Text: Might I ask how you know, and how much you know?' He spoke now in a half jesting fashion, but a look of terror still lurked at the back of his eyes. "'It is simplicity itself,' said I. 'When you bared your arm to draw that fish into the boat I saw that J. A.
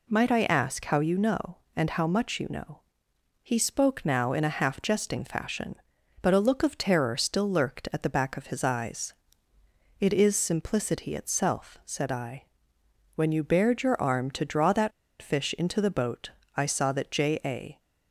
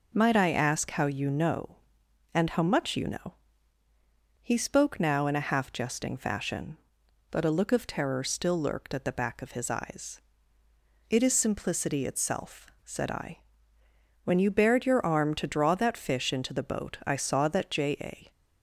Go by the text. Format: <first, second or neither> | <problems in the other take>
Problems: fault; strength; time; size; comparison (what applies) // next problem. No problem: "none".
second | pauses between "that" and "fish"; slight; at 14.9 s; 0.31 s long // pauses between "boat" and "I"; slight; at 16.3 s; 0.26 s long